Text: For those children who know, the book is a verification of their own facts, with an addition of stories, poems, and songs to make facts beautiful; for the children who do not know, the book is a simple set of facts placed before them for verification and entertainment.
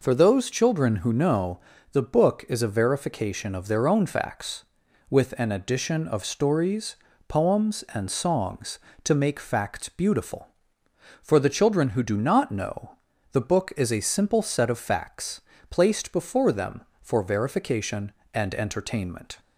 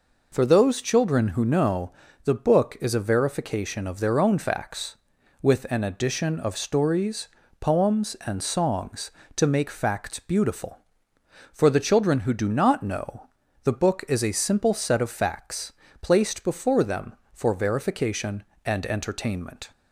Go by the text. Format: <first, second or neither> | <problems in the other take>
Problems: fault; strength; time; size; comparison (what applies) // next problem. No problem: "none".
neither | pauses between "facts" and "placed"; slight; the same in both